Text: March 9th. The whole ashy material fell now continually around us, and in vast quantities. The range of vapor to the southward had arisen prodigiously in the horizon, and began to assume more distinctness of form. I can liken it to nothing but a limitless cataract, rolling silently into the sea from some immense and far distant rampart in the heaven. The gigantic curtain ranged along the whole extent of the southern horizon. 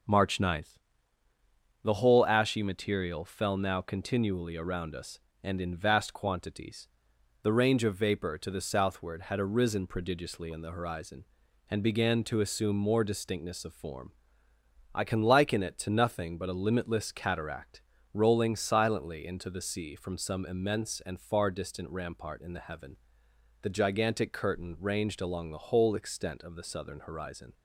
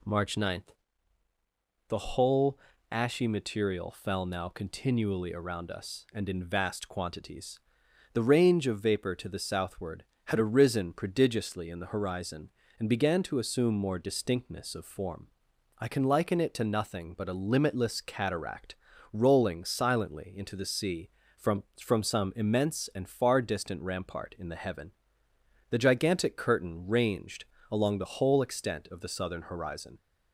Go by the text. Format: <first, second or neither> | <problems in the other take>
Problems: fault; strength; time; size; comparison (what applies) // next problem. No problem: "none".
first | pauses between "whole" and "ashy"; slight; at 2.5 s; 0.32 s long // says "from" twice; at 21.7 s // pauses between "ranged" and "along"; slight; at 27.4 s; 0.28 s long